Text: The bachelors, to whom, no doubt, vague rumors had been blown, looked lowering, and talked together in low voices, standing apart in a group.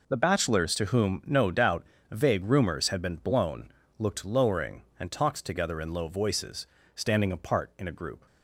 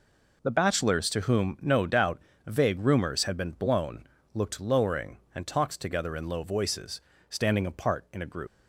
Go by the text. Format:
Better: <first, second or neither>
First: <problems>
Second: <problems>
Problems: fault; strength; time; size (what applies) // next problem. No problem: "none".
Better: first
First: none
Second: leaves "group" unfinished; at 8.4 s; 130 ms